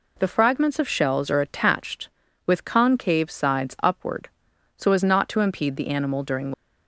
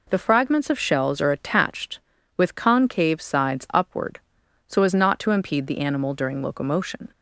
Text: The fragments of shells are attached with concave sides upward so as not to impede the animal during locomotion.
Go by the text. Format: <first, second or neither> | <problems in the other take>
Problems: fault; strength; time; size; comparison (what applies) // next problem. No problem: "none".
second | stops before "locomotion"; at 6.5 s